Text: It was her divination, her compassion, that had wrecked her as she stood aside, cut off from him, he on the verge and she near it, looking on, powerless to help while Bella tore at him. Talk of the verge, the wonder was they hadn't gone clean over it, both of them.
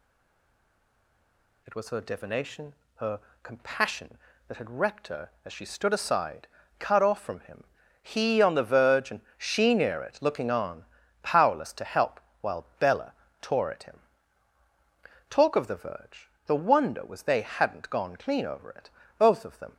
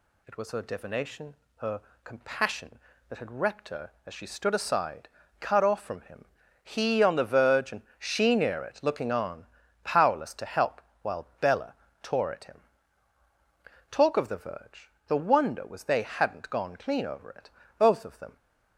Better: second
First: stays silent before the first word; noticeable; until 1.6 s; 1.6 s long // pauses between "her" and "compassion"; slight; at 3.2 s; 0.22 s long // pauses between "and" and "she"; slight; at 9.2 s; 0.16 s long // pauses between "help" and "while"; slight; at 12.1 s; 0.22 s long // pauses between "Bella" and "tore"; slight; at 13.1 s; 0.30 s long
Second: pauses between "her" and "compassion"; slight; at 1.8 s; 0.22 s long // pauses between "and" and "she"; slight; at 7.8 s; 0.16 s long // pauses between "help" and "while"; slight; at 10.7 s; 0.22 s long // pauses between "Bella" and "tore"; slight; at 11.7 s; 0.30 s long

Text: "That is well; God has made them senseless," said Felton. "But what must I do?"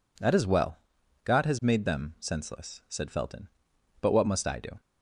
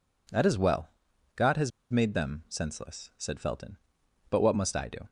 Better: first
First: none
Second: pauses between "has" and "made"; slight; at 1.7 s; 0.20 s long

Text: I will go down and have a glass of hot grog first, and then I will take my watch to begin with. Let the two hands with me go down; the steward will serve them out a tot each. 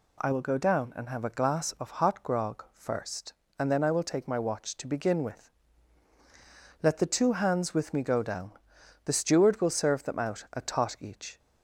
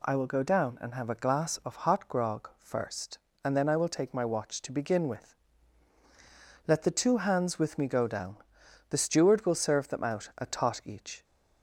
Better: neither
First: none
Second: none

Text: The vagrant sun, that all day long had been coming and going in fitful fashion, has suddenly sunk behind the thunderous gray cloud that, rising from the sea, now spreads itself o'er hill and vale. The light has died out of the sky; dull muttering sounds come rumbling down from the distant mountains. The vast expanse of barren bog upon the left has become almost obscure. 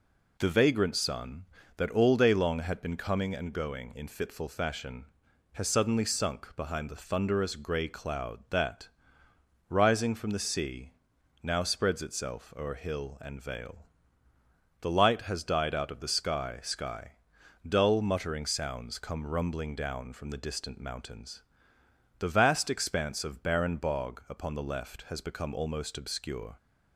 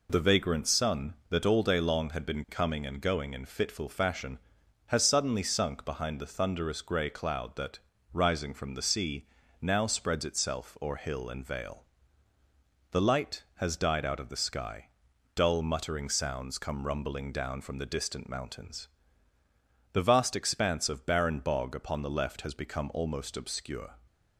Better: second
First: says "sky" twice; at 16.6 s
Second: none

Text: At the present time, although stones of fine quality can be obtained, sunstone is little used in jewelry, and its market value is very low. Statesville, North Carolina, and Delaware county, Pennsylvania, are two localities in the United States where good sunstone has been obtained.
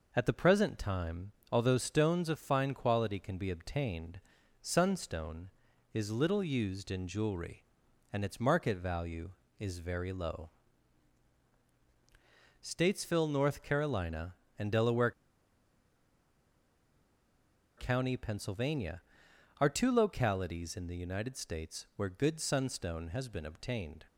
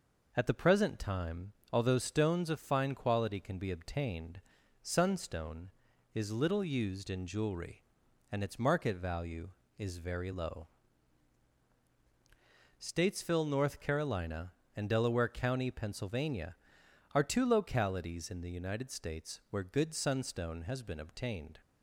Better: second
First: pauses between "Delaware" and "county"; strong; at 15.1 s; 2.6 s long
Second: none

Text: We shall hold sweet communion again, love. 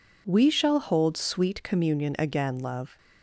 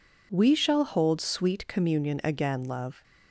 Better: neither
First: none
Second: none

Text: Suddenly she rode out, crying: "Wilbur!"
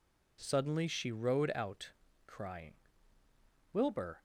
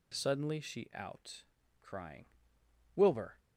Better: first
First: none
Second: skips "rode"; at 0.9 s

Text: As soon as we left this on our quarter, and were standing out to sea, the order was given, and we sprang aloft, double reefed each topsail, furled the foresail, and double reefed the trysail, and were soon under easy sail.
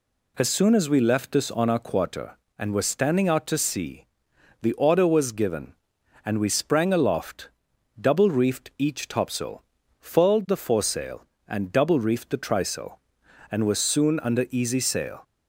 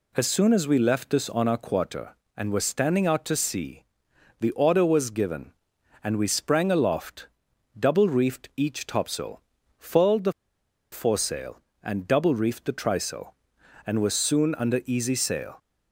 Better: first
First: none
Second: pauses between "the" and "foresail"; noticeable; at 10.3 s; 0.59 s long

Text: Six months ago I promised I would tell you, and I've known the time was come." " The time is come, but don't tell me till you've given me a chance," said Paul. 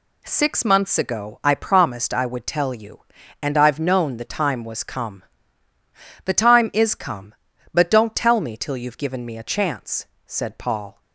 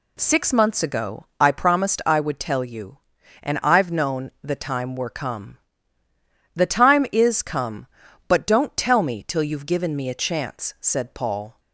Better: first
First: none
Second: says "were" for "was"; at 4.9 s

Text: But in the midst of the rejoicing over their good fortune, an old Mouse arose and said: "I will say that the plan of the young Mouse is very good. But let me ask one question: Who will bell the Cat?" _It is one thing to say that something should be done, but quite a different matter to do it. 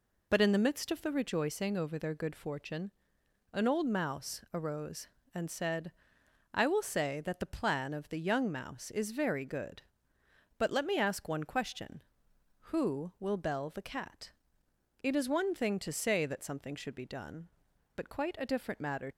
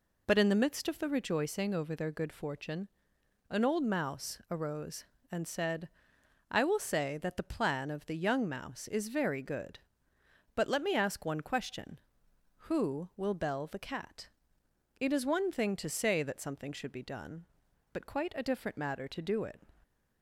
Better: second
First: stops before "to do it"; at 19.1 s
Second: none

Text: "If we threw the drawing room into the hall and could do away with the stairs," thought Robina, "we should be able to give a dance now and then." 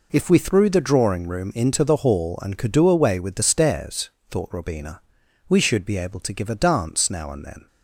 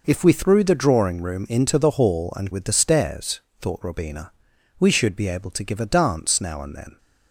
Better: first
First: none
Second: skips "could do away"; at 2.5 s

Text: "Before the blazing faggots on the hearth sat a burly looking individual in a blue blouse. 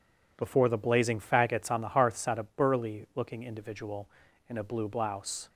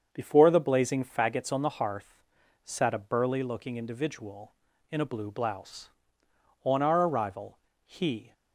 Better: first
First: none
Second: starts louder than the rest; until 1.1 s; 7 dB // pauses between "hearth" and "sat"; noticeable; at 2.1 s; 0.48 s long // goes on to say "On our arrival he"; strong; from 6.6 s on; 1.6 s long

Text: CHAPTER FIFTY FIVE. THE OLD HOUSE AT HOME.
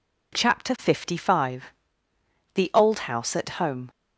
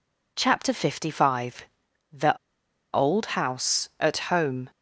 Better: first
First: none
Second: pauses between "THE" and "OLD"; noticeable; at 2.3 s; 0.61 s long

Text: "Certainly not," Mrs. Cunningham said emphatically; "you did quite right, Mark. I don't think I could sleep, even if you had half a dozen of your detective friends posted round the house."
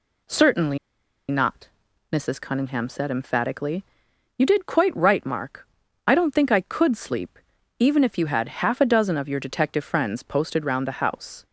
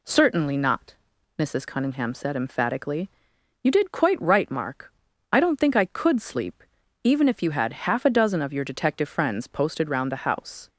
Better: second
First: pauses between "Certainly" and "not"; noticeable; at 0.7 s; 0.52 s long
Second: none

